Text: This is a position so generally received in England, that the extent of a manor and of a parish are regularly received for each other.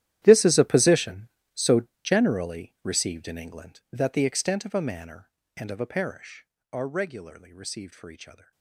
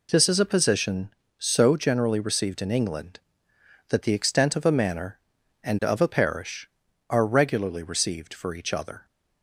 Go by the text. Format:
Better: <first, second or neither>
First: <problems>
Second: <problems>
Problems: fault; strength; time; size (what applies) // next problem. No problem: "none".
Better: second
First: gets quieter; strong; throughout; 18.5 dB // pauses between "so" and "generally"; slight; at 1.8 s; 0.22 s long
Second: none